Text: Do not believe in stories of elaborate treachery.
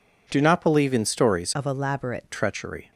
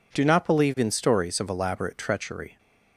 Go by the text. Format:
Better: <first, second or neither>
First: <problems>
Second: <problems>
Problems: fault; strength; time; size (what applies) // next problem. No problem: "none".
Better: second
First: changes voice from "of" to "elaborate"; from 1.5 to 2.2 s; 0.7 s long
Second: none